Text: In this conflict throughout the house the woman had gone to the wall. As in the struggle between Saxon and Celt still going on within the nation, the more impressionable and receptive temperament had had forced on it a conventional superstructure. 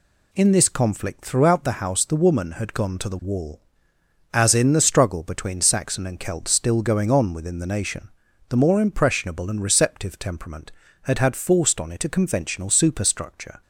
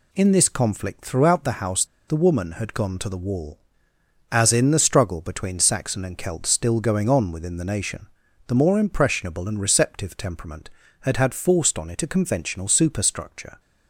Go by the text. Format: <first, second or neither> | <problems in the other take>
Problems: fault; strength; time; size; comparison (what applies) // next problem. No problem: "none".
first | pauses between "house" and "the"; slight; at 1.8 s; 0.22 s long